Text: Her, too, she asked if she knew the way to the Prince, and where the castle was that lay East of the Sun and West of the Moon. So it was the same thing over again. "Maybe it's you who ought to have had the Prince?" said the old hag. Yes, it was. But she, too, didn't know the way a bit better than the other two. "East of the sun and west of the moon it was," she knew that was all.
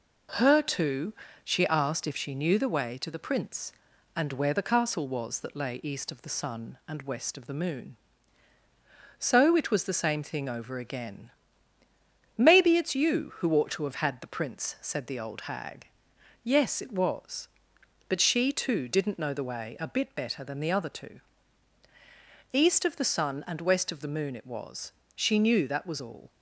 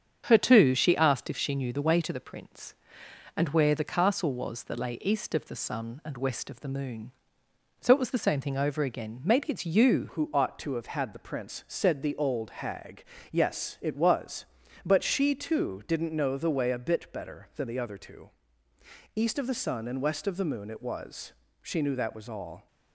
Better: first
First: none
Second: starts louder than the rest; strong; until 1.2 s; 7.5 dB // changes voice at "who"; from 10.1 s on; 12.5 s long

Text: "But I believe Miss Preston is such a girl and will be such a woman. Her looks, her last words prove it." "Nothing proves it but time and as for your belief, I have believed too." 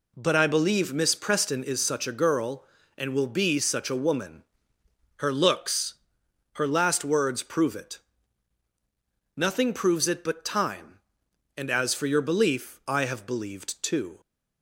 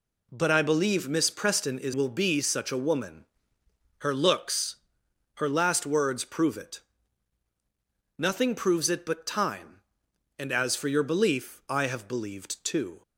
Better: first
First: none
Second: skips "such a girl and"; at 1.9 s

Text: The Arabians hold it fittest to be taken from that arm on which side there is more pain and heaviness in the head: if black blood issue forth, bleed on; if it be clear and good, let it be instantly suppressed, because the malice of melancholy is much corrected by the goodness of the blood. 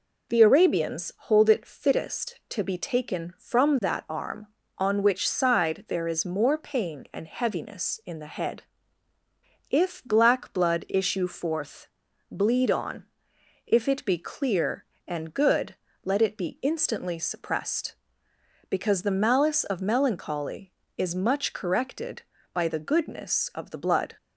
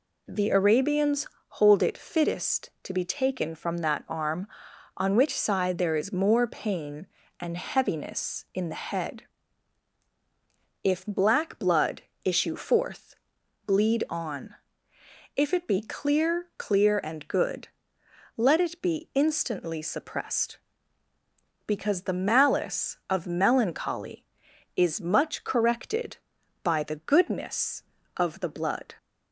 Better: first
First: none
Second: pauses between "Arabians" and "hold"; slight; at 1.2 s; 0.22 s long // pauses between "blood" and "issue"; slight; at 11.9 s; 0.24 s long // says "clear" twice; at 16.5 s

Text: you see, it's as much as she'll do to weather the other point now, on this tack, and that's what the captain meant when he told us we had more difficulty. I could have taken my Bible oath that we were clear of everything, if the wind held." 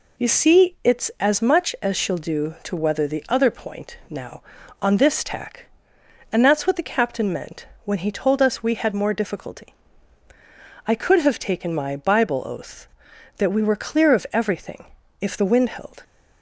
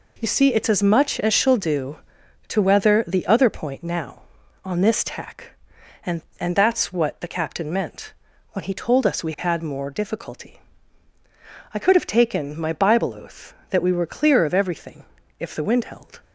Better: first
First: pauses between "meant" and "when"; slight; at 7.6 s; 0.18 s long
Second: says "and" twice; at 6.3 s // pauses between "meant" and "when"; at 8.1 s; 0.40 s long

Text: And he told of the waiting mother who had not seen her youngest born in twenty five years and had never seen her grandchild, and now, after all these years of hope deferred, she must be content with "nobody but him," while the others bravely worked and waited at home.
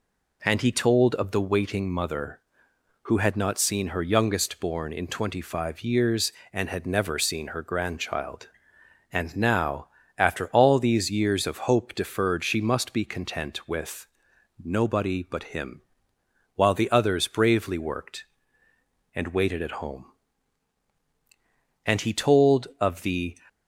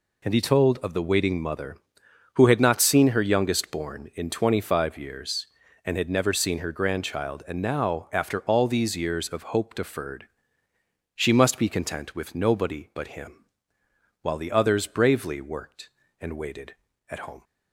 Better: second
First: pauses between "with" and "nobody"; noticeable; at 14.0 s; 0.56 s long // goes on to say "And he told of the"; from 21.8 s on; 1.5 s long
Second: none

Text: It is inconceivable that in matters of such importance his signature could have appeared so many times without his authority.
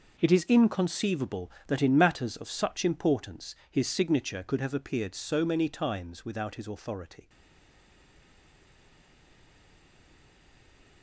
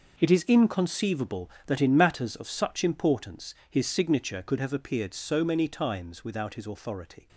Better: second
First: stays silent after the last word; strong; from 7.2 s on; 3.8 s long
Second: none

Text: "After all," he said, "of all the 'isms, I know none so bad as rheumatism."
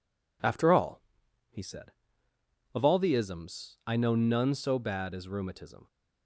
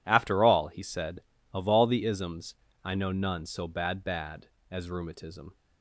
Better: first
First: none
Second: says "bad" twice; at 4.0 s

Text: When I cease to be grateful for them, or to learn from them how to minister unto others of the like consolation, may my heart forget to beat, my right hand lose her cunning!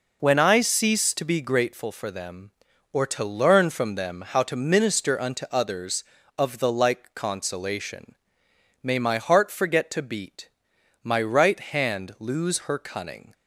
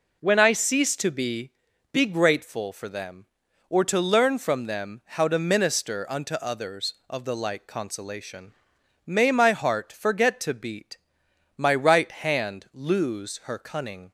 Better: first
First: none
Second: says "be" twice; at 1.9 s

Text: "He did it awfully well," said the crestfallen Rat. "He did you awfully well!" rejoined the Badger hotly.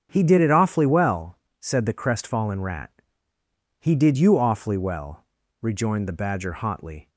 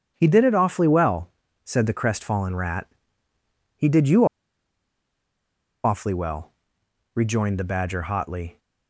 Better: first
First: starts louder than the rest; strong; until 1.1 s; 7.5 dB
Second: starts louder than the rest; strong; until 1.1 s; 9 dB // pauses between "you" and "awfully"; strong; at 4.2 s; 1.5 s long

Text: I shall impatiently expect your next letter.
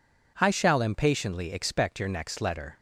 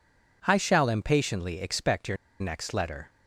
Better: first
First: none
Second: pauses between "your" and "next"; slight; at 2.1 s; 0.24 s long

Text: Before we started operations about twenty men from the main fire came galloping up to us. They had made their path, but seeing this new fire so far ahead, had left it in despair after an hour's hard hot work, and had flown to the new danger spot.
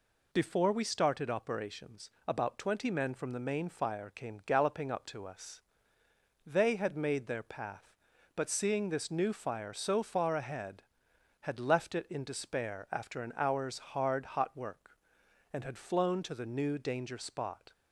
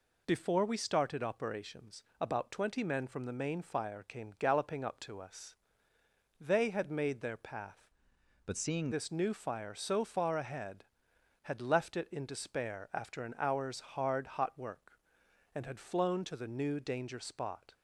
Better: first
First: pauses between "operations" and "about"; slight; at 2.0 s; 0.16 s long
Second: pauses between "operations" and "about"; slight; at 2.0 s; 0.16 s long // changes voice from "but" to "seeing"; from 8.4 to 8.8 s; 0.4 s long

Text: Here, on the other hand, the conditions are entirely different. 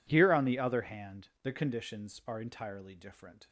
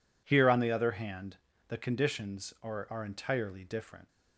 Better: first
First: none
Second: says "are" twice; at 2.8 s

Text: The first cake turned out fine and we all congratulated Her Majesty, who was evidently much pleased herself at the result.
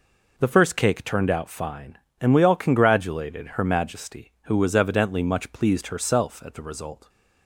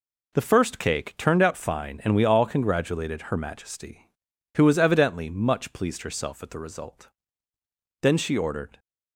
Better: first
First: none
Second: goes on to say "Then she ordered"; noticeable; from 8.0 s on; 0.76 s long

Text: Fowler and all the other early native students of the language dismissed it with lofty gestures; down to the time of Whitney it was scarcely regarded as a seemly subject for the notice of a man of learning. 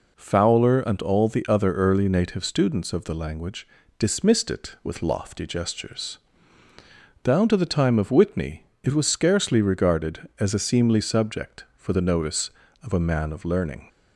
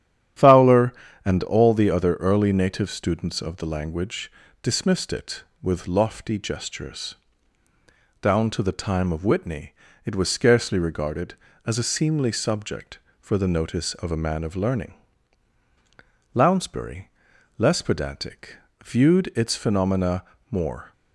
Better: first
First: pauses between "language" and "dismissed"; slight; at 3.6 s; 0.32 s long // pauses between "Whitney" and "it"; slight; at 8.6 s; 0.20 s long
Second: starts louder than the rest; strong; until 1.7 s; 10 dB // pauses between "language" and "dismissed"; slight; at 4.3 s; 0.30 s long // pauses between "Whitney" and "it"; slight; at 9.7 s; 0.32 s long // goes on to say "Lounsbury less pedantic viewed its phenomena more"; strong; from 16.3 s on; 4.5 s long

